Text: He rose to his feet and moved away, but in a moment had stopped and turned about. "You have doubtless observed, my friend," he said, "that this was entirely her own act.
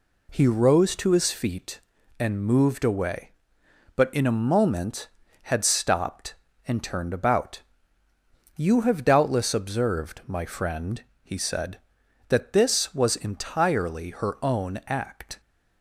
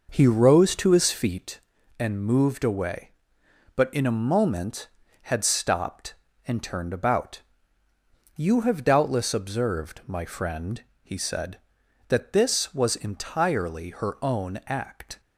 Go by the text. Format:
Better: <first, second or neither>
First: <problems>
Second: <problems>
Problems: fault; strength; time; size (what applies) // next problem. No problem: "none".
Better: first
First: none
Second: starts louder than the rest; noticeable; until 1.5 s; 5.5 dB